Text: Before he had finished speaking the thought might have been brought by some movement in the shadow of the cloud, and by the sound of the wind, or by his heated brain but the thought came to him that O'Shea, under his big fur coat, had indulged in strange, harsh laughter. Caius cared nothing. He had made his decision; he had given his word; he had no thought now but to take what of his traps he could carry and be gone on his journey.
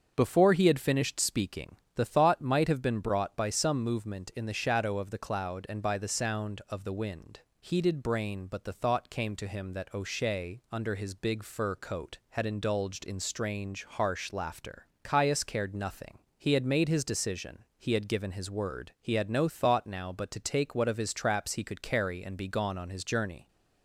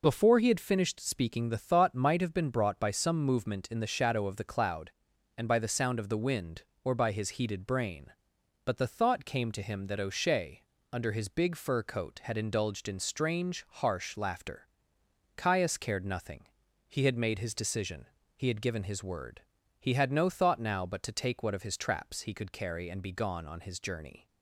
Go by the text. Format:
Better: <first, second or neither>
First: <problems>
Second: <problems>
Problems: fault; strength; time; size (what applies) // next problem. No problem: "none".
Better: second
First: starts louder than the rest; until 1.1 s; 6.5 dB // pauses between "speaking" and "the"; slight; at 1.7 s; 0.20 s long // skips "or by his"; at 7.4 s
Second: none